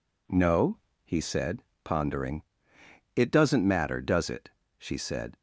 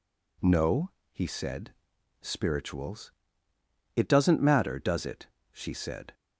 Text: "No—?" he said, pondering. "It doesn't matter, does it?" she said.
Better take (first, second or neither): first